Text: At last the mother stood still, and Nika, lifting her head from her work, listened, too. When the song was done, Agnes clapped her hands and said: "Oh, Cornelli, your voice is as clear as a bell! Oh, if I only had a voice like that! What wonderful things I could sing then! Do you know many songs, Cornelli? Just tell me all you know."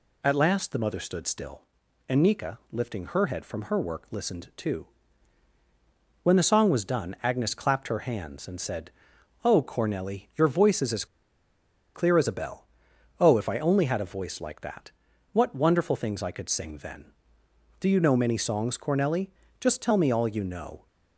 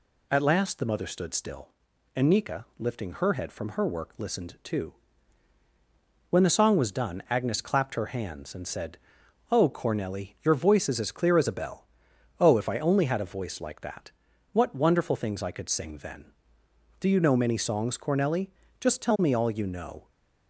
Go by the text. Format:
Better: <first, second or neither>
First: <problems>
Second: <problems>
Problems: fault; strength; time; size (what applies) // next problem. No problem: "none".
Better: second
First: pauses between "as" and "clear"; noticeable; at 11.0 s; 0.89 s long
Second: none